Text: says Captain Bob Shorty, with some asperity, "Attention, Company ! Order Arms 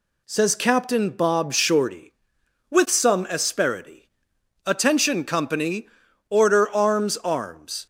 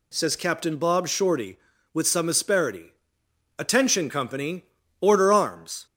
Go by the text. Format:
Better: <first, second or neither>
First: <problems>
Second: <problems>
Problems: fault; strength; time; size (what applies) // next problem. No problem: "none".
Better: second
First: says "Arms" twice; at 7.1 s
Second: none